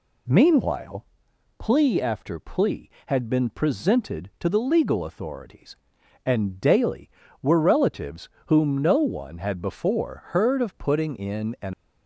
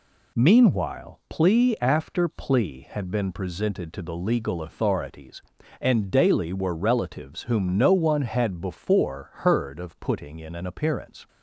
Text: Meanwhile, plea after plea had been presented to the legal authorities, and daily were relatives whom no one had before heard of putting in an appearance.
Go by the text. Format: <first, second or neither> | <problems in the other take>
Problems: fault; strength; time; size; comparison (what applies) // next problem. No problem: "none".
second | pauses between "relatives" and "whom"; slight; at 8.2 s; 0.18 s long // stops before "appearance"; at 11.7 s